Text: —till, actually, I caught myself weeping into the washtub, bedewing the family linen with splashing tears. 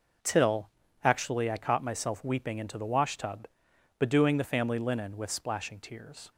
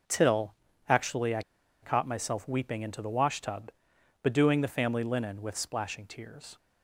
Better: first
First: none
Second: pauses between "I" and "caught"; at 1.4 s; 0.41 s long

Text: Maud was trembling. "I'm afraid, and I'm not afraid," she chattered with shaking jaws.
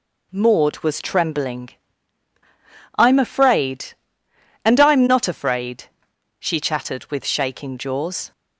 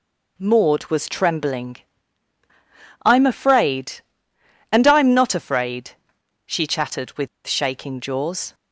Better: first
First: none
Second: pauses between "with" and "shaking"; slight; at 7.2 s; 0.17 s long

